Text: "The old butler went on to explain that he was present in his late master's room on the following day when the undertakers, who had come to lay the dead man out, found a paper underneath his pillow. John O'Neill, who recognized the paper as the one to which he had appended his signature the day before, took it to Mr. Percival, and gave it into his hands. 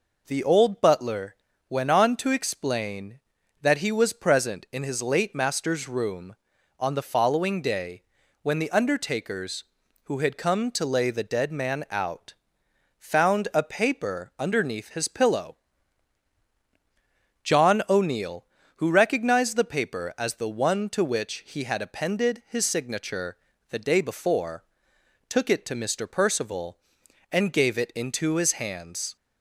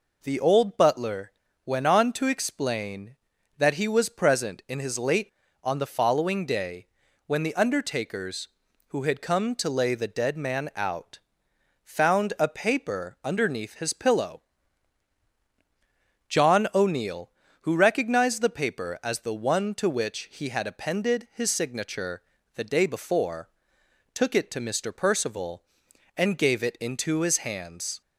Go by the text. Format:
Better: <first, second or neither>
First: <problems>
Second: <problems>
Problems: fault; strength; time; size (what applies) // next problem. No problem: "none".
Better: first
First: pauses between "butler" and "went"; slight; at 1.3 s; 0.34 s long // pauses between "day" and "when"; at 8.0 s; 0.40 s long // pauses between "signature" and "the"; slight; at 23.3 s; 0.32 s long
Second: pauses between "butler" and "went"; slight; at 1.3 s; 0.34 s long // skips "master's room"; at 5.4 s // pauses between "day" and "when"; at 6.8 s; 0.40 s long // pauses between "signature" and "the"; slight; at 22.2 s; 0.32 s long